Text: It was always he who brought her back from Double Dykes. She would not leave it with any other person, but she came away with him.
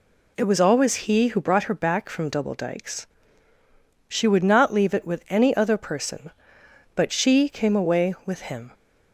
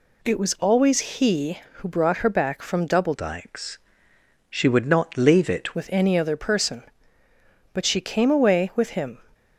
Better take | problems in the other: first | changes voice from "Dykes" to "it"; from 3.1 to 5.7 s; 2.6 s long

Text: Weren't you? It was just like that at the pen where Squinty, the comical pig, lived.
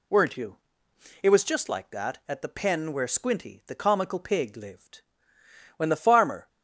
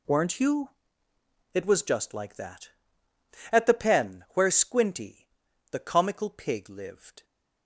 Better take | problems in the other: second | goes on to say "When the farmer"; noticeable; from 5.7 s on; 0.72 s long

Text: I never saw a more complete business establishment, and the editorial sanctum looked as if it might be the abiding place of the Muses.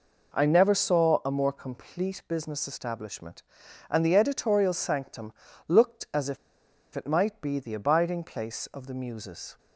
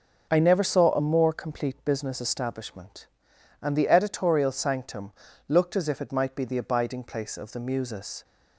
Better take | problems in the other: second | pauses between "sanctum" and "looked"; slight; at 5.3 s; 0.36 s long; also in the second // pauses between "if" and "it"; noticeable; at 6.3 s; 0.58 s long

